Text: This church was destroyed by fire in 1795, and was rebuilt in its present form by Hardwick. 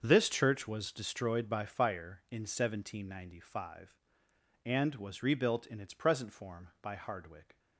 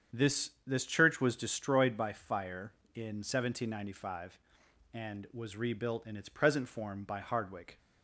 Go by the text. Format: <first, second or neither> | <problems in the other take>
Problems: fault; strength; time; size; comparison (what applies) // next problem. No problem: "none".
first | starts louder than the rest; strong; until 1.2 s; 7.5 dB; also in the first // says "This" twice; at 0.6 s